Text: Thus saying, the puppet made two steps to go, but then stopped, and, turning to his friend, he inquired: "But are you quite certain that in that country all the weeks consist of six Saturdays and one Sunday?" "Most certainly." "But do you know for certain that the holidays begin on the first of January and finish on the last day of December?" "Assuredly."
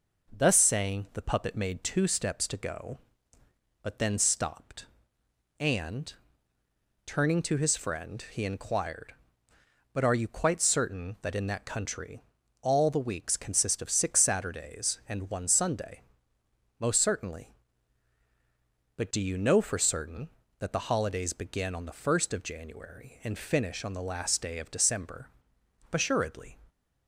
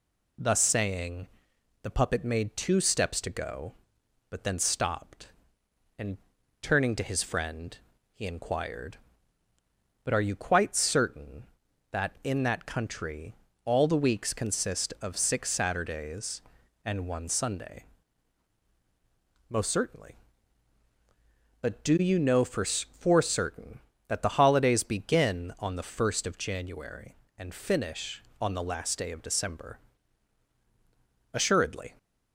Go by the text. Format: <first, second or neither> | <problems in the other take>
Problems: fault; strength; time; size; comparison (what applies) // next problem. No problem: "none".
first | pauses between "country" and "all"; slight; at 13.3 s; 0.30 s long; also in the first // says "for" twice; at 22.6 s